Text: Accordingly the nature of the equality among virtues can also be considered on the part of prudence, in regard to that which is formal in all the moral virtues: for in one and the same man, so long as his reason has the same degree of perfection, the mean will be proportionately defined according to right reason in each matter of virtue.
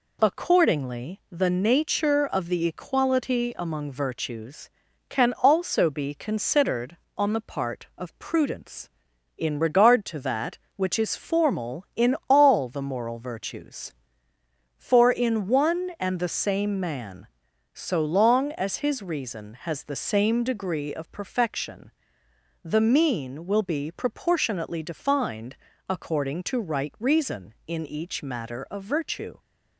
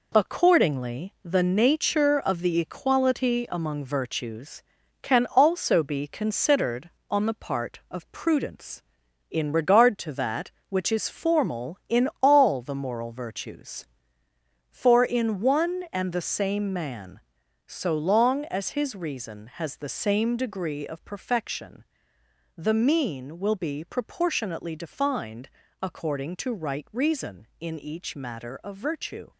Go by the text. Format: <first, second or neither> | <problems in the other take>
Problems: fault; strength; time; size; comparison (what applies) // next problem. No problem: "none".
first | gets quieter; noticeable; throughout; 6 dB // pauses between "defined" and "according"; slight; at 25.4 s; 0.32 s long; slight in the first